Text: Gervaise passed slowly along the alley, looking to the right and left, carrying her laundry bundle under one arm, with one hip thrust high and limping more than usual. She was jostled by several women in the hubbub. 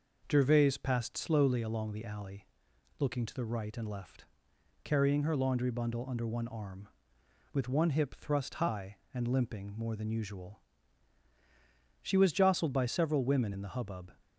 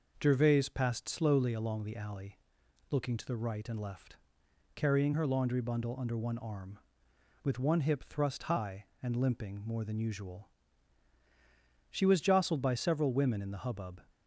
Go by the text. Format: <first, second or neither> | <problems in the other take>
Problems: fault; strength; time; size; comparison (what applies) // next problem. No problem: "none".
neither | none